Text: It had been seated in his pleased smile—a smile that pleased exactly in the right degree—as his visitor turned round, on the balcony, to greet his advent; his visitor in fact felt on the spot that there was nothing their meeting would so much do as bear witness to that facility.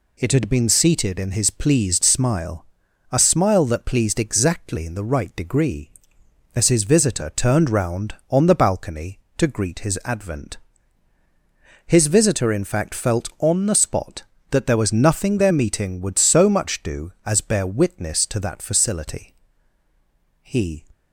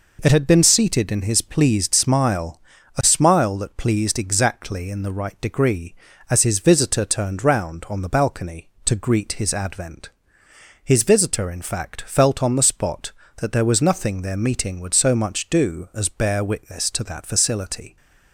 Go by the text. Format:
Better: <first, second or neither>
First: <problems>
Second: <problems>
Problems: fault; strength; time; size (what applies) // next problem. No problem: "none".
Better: second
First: goes on to say "He"; slight; from 20.4 s on; 0.44 s long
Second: none